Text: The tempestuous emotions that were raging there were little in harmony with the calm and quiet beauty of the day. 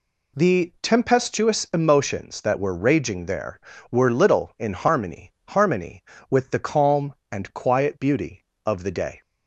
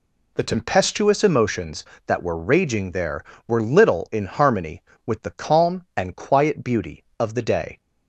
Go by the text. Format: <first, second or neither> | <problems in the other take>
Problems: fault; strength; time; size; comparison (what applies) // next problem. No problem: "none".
second | says "harmony" twice; at 5.4 s